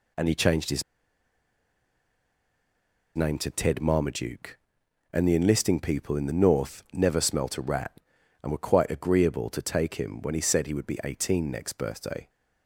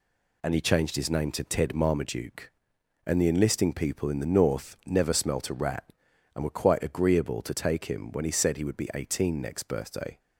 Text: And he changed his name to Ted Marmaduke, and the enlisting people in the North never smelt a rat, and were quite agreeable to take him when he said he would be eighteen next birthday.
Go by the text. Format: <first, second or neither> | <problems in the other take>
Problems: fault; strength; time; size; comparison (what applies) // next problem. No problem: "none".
second | pauses between "his" and "name"; strong; at 0.8 s; 2.3 s long